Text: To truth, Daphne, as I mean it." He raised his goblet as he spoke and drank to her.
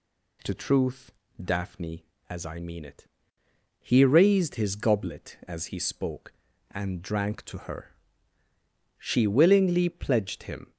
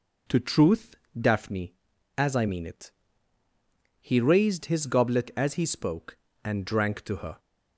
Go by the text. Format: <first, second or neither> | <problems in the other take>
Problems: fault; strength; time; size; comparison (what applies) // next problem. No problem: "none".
second | goes on to say "She willingly pledged him"; strong; from 8.9 s on; 1.7 s long